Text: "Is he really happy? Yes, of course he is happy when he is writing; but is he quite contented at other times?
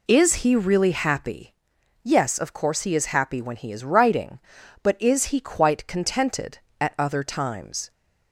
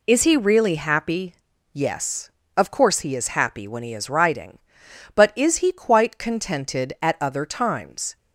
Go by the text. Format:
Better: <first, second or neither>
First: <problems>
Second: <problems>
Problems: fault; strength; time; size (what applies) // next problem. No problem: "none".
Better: neither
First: none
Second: none